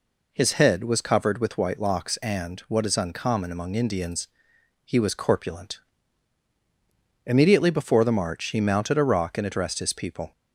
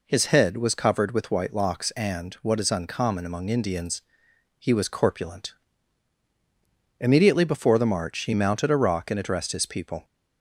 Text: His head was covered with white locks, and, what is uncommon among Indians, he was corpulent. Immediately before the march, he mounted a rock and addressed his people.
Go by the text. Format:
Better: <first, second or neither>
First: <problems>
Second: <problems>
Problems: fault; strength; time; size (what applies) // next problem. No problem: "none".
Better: neither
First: none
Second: none